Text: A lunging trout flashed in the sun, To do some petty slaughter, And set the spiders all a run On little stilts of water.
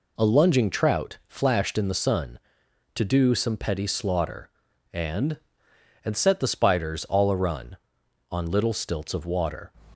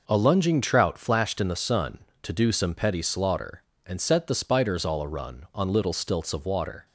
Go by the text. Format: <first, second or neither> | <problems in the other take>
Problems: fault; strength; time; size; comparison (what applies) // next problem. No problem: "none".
second | says "And" twice; at 6.0 s